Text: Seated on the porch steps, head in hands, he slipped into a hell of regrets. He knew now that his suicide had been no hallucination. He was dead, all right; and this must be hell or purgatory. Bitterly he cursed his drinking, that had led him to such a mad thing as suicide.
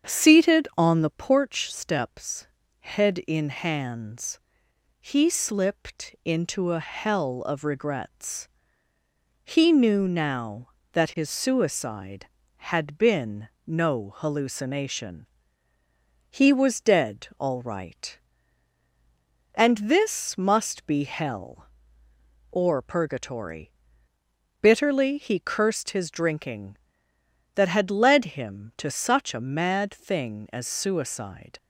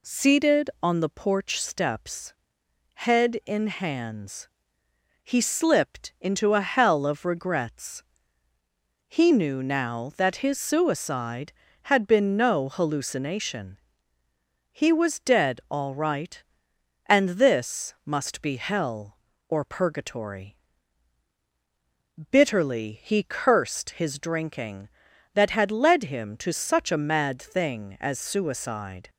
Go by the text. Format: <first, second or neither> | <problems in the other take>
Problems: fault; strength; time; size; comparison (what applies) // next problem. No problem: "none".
second | starts louder than the rest; strong; until 1.5 s; 7.5 dB // pauses between "been" and "no"; slight; at 13.4 s; 0.18 s long